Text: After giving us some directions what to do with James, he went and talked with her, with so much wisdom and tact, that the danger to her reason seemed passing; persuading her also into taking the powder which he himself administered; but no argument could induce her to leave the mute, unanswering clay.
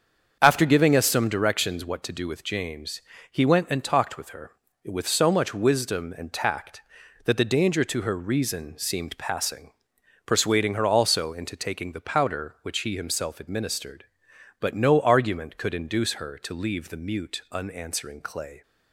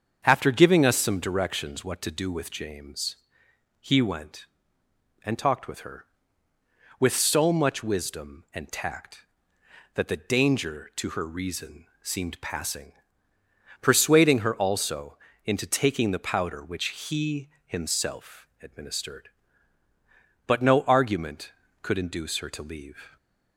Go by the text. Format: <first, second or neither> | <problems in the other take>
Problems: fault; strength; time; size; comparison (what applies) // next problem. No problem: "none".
first | starts louder than the rest; until 1.2 s; 7 dB; also in the first // pauses between "reason" and "seemed"; slight; at 11.8 s; 0.16 s long // pauses between "also" and "into"; slight; at 15.1 s; 0.28 s long // pauses between "he" and "himself"; slight; at 17.4 s; 0.18 s long // pauses between "himself" and "administered"; slight; at 18.4 s; 0.16 s long // stops before "the mute unanswering clay"; at 23.1 s